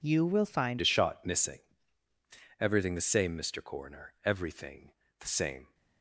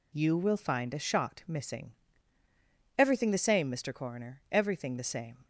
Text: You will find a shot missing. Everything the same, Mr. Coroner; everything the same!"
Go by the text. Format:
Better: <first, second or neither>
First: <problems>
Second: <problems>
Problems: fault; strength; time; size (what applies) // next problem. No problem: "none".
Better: second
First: changes voice at "a"; from 0.8 s on; 4.9 s long // pauses between "everything" and "the"; slight; at 4.9 s; 0.26 s long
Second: none